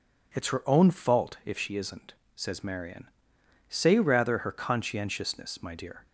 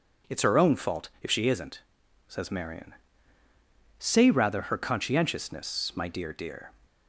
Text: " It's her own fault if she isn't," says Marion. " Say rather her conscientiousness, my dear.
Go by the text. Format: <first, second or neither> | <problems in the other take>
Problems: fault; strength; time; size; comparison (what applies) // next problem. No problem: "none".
first | says "dear" twice; at 6.3 s